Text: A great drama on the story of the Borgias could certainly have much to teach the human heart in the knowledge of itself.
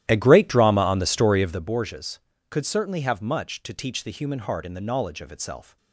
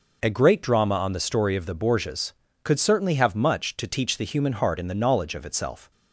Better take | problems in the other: second | starts louder than the rest; strong; until 1.8 s; 13.5 dB

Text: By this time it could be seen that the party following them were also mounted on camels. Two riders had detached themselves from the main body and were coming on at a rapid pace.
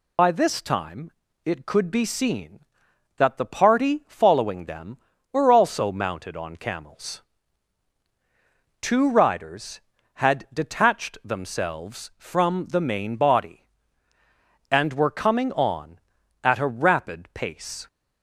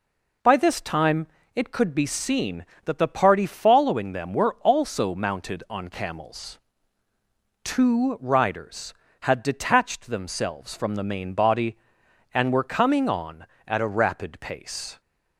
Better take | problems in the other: second | loses the start of "By"; at 0.1 s; 120 ms // pauses between "time" and "it"; slight; at 1.1 s; 0.34 s long; slight in the second

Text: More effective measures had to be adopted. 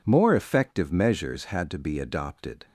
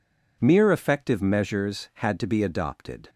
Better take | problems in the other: first | says "Mere" for "More"; at 0.4 s

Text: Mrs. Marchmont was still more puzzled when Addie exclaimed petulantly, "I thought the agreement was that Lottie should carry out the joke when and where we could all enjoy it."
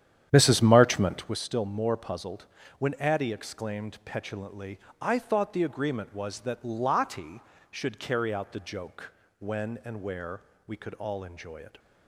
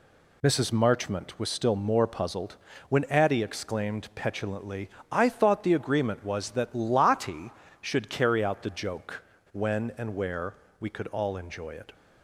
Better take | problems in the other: second | starts louder than the rest; strong; until 1.4 s; 10 dB // pauses between "puzzled" and "when"; slight; at 2.4 s; 0.32 s long; slight in the second // pauses between "joke" and "when"; slight; at 9.1 s; 0.28 s long; slight in the second // pauses between "where" and "we"; slight; at 10.4 s; 0.26 s long; slight in the second

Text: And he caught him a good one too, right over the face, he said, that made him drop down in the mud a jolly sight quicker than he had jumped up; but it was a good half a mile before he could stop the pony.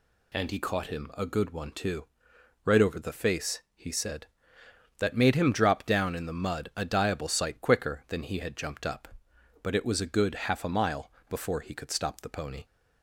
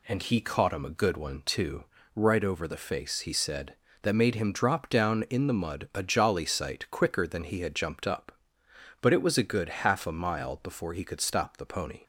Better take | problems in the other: second | says "diable" for "jolly"; at 6.8 s // pauses between "mile" and "before"; slight; at 11.1 s; 0.18 s long

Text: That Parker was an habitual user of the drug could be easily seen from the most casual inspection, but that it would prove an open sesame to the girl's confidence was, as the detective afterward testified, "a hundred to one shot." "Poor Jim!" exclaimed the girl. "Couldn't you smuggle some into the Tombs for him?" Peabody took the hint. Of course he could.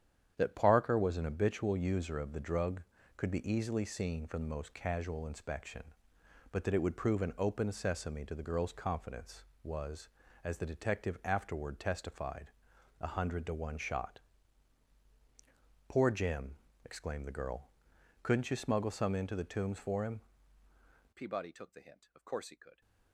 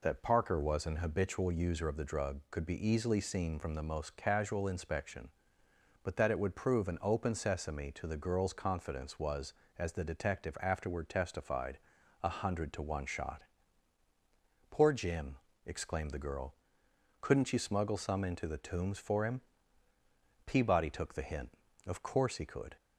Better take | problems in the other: second | starts louder than the rest; strong; until 1.3 s; 9 dB // changes voice at "Peabody"; from 21.1 s on; 1.7 s long

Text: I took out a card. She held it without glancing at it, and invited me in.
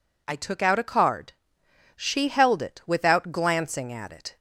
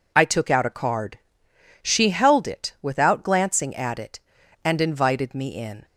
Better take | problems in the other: second | stops before "and invited me in"; at 4.3 s

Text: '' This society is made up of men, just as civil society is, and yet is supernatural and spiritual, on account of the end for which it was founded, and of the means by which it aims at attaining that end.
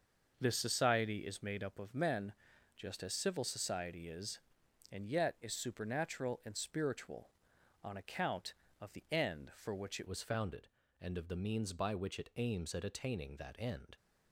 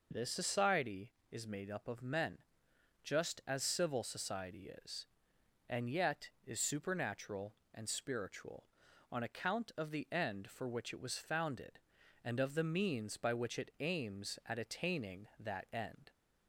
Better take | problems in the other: second | starts louder than the rest; until 1.3 s; 6 dB // changes voice at "was"; from 10.0 s on; 3.9 s long

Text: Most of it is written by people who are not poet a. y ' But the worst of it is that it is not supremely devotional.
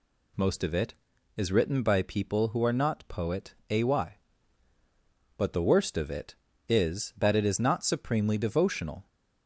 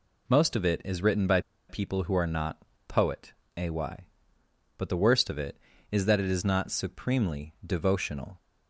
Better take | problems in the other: first | pauses between "by" and "people"; slight; at 1.3 s; 0.29 s long // pauses between "not" and "poet"; slight; at 2.5 s; 0.28 s long // pauses between "poet" and "a"; slight; at 3.3 s; 0.24 s long; slight in the first

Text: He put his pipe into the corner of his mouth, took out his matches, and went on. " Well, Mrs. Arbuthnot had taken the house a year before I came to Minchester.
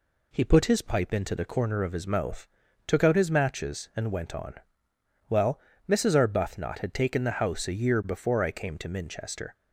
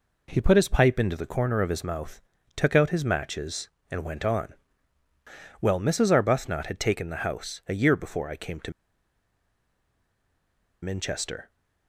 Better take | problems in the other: first | pauses between "to" and "Minchester"; strong; at 8.7 s; 2.1 s long

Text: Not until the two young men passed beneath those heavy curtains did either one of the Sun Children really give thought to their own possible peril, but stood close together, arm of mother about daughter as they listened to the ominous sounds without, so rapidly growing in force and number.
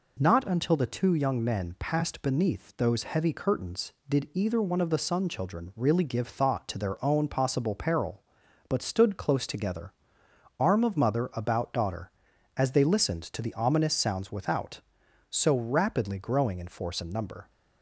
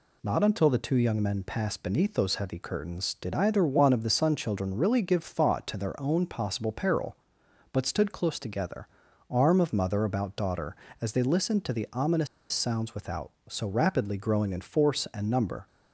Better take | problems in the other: first | pauses between "ominous" and "sounds"; slight; at 12.2 s; 0.25 s long

